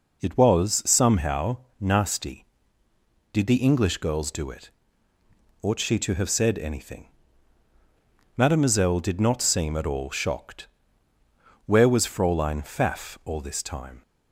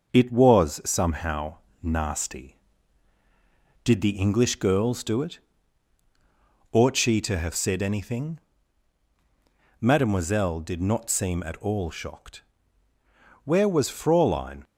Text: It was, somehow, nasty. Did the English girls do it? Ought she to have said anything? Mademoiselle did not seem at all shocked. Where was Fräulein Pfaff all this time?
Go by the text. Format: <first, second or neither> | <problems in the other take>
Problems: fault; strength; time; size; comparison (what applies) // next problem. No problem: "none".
first | starts louder than the rest; noticeable; until 1.1 s; 6 dB // stops before "Pfaff all this time"; at 14.6 s